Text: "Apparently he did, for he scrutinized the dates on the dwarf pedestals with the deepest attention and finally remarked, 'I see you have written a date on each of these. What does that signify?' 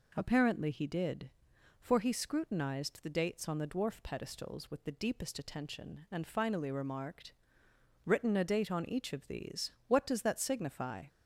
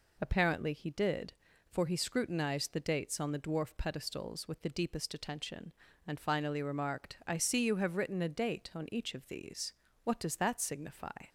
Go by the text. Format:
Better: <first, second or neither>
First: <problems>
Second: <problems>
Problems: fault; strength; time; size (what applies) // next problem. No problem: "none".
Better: second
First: skips "I see you have"; at 7.6 s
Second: none